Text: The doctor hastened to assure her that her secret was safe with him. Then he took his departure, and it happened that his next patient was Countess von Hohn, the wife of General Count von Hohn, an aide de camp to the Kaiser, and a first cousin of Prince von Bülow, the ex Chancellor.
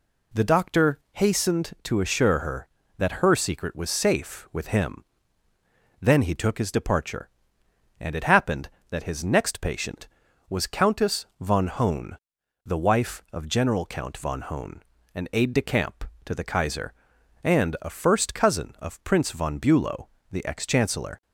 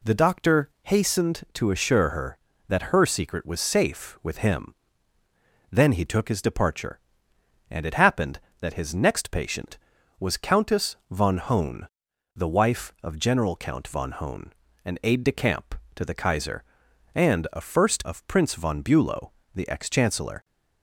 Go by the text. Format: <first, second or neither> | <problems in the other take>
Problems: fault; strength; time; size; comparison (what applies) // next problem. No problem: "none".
first | skips "cousin"; at 18.0 s